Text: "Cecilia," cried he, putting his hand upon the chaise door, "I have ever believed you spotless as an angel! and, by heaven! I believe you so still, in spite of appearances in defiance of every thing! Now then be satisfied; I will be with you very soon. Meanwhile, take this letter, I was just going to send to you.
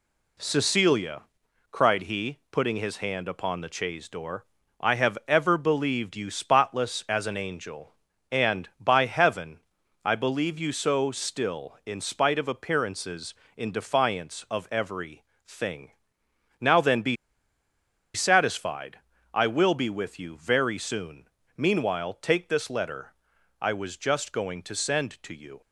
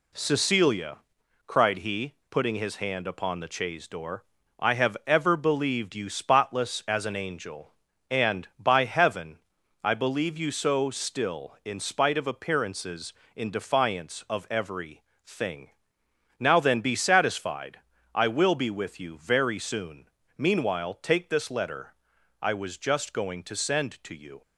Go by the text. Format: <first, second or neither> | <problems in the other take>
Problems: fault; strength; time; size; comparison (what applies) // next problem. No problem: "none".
second | pauses between "every" and "thing"; slight; at 15.2 s; 0.20 s long; slight in the second // pauses between "be" and "satisfied"; at 17.1 s; 0.98 s long